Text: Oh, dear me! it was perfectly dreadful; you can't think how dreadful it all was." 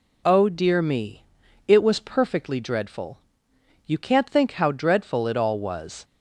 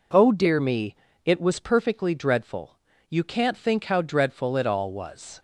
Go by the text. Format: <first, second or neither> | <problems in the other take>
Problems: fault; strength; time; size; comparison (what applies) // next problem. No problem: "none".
neither | none